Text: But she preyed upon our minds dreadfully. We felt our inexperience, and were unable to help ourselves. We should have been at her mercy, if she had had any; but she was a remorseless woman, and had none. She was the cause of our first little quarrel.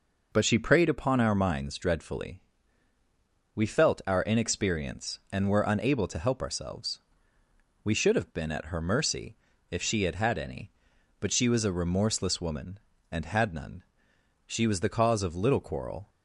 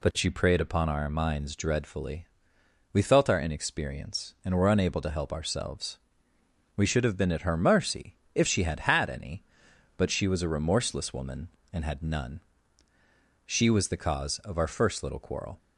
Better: second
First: skips "our first"; at 15.3 s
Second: none

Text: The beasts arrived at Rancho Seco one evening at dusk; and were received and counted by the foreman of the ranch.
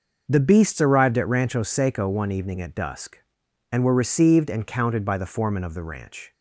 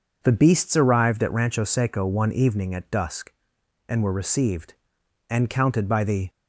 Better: first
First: none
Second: stops before "foreman of the ranch"; at 6.2 s

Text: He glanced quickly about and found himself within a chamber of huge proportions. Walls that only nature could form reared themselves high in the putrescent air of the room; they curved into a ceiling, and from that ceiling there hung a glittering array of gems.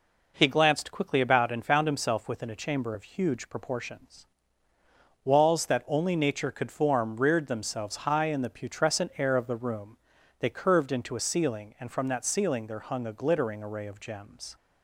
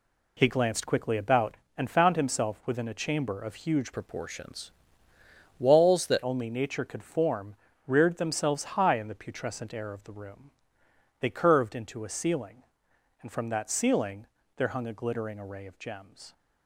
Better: first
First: none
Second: changes voice from "proportions" to "that"; from 3.9 to 6.1 s; 2.2 s long // pauses between "form" and "reared"; slight; at 7.5 s; 0.32 s long // pauses between "ceiling" and "there"; slight; at 14.2 s; 0.30 s long

